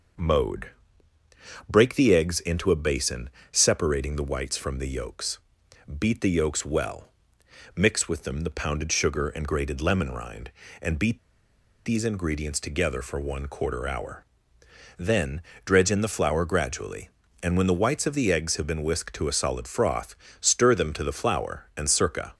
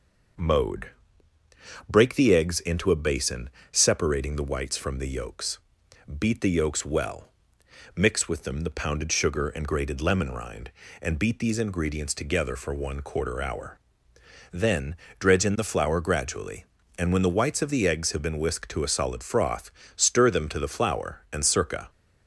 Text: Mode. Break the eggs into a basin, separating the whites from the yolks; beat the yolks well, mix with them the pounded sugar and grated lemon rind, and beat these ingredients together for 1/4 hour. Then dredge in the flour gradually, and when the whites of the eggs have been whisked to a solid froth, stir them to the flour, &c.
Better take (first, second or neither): second